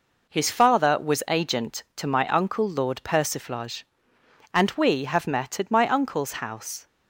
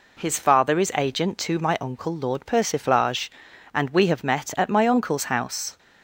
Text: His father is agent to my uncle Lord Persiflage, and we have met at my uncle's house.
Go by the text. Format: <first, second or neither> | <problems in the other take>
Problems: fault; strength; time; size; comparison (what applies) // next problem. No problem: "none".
second | says "was" for "is"; at 0.9 s